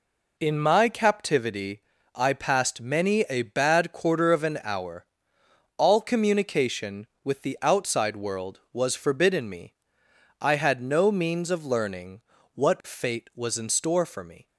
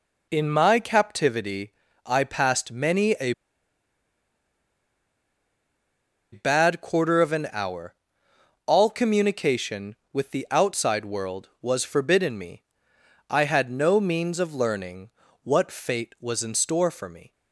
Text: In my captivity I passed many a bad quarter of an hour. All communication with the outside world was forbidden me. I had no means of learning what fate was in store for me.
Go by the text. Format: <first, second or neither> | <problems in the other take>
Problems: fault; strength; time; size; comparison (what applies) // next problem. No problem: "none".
first | pauses between "captivity" and "I"; slight; at 1.7 s; 0.32 s long; slight in the first // pauses between "a" and "bad"; strong; at 3.3 s; 3.0 s long // pauses between "learning" and "what"; slight; at 15.0 s; 0.32 s long; slight in the first